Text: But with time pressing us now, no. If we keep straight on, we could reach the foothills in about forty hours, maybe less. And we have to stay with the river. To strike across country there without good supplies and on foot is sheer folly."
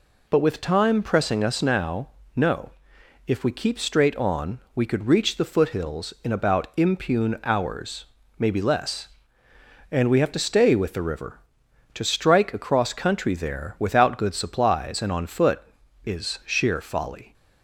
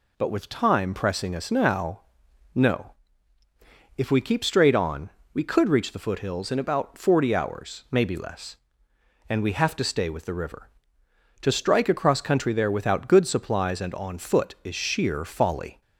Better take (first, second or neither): second